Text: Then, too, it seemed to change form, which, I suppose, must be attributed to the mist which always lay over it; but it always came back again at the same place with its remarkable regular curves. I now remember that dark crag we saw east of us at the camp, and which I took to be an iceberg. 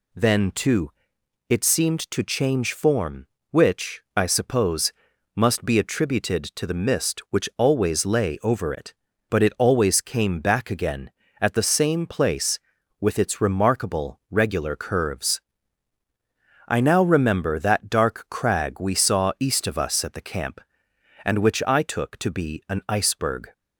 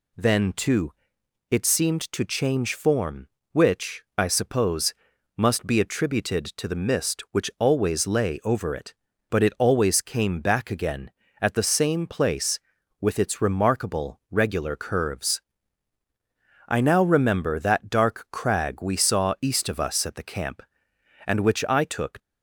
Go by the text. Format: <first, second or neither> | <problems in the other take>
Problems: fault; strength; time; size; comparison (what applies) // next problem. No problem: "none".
first | stops before "to be an iceberg"; at 22.1 s